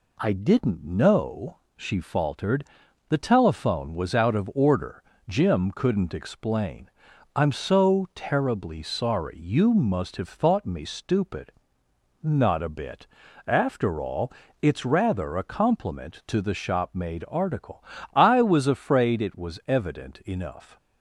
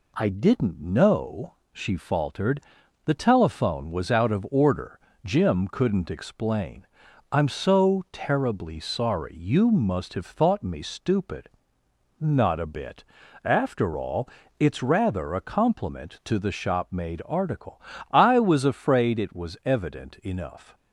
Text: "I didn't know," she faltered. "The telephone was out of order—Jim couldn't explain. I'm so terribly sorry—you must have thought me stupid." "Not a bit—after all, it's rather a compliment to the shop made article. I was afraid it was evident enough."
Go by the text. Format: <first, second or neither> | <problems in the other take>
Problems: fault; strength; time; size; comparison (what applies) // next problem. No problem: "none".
neither | none